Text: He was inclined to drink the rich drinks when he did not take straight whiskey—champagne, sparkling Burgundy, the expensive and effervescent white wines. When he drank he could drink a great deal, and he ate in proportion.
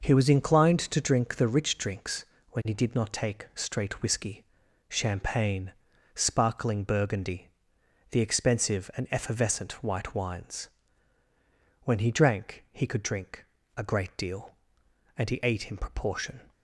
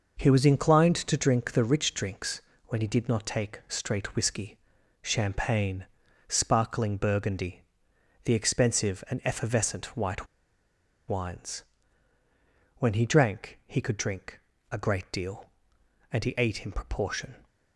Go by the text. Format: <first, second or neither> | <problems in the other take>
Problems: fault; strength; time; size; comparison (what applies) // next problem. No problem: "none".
first | pauses between "drinks" and "when"; slight; at 2.4 s; 0.24 s long; slight in the first // pauses between "white" and "wines"; noticeable; at 10.2 s; 0.81 s long // pauses between "drink" and "a"; slight; at 14.4 s; 0.30 s long; slight in the first